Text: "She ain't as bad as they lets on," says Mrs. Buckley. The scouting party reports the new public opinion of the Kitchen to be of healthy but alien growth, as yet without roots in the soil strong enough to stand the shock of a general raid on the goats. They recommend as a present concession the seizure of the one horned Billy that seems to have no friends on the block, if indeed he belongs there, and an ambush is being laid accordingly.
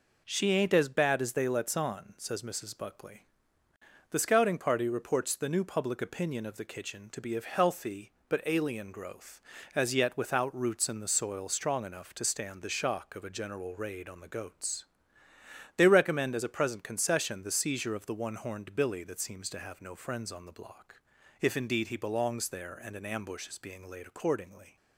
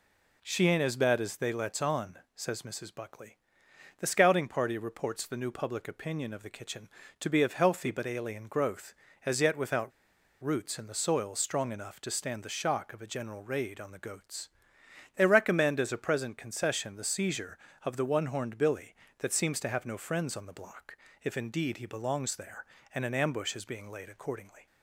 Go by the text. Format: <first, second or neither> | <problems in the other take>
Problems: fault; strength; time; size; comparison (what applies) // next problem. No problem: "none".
first | pauses between "without" and "roots"; noticeable; at 9.9 s; 0.52 s long